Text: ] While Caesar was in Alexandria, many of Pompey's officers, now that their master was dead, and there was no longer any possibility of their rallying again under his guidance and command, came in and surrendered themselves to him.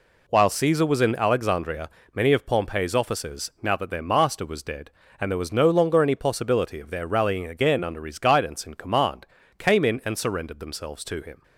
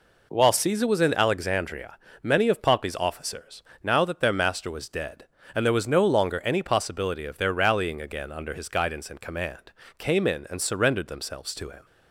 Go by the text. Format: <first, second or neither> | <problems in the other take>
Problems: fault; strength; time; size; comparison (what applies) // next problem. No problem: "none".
neither | none